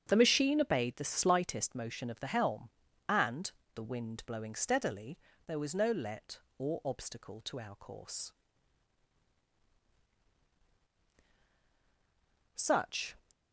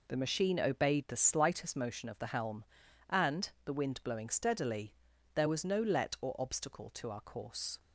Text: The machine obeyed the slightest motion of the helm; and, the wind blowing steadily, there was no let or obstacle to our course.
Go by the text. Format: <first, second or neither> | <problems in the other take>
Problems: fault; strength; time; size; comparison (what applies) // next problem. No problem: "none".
second | starts louder than the rest; strong; until 1.0 s; 7.5 dB // goes on to say "Such"; noticeable; from 12.5 s on; 0.62 s long